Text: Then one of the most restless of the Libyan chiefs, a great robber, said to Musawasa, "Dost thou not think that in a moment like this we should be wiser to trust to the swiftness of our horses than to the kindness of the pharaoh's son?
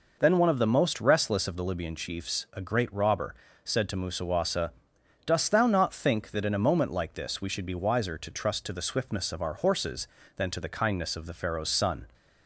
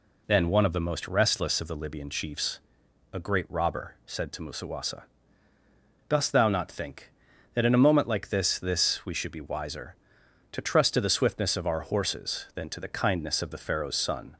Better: first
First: none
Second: says "this" twice; at 8.5 s

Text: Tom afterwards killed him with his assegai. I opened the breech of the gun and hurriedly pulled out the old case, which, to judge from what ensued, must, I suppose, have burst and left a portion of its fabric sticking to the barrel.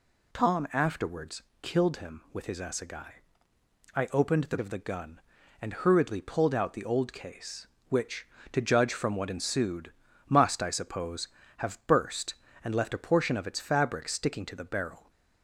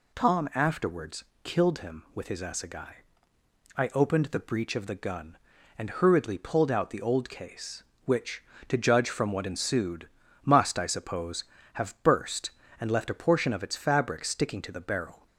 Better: second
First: pauses between "afterwards" and "killed"; slight; at 1.4 s; 0.18 s long // skips "breech"; at 4.5 s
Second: pauses between "afterwards" and "killed"; slight; at 1.2 s; 0.18 s long

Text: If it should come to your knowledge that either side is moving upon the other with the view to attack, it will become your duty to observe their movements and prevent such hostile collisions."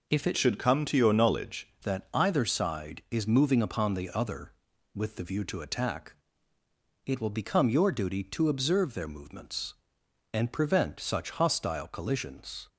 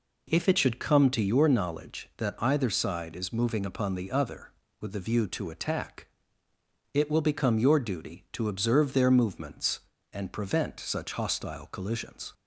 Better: second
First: changes voice from "should" to "knowledge"; from 0.3 to 1.6 s; 1.3 s long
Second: none

